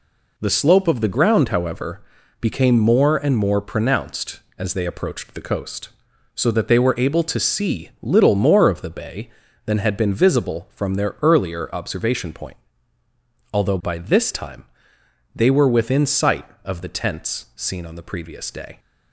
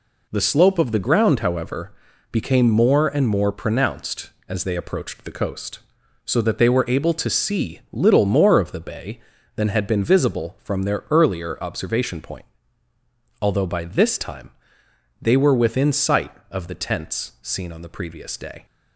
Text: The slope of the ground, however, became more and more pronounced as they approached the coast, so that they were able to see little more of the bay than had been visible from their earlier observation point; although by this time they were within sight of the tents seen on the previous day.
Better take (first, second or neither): neither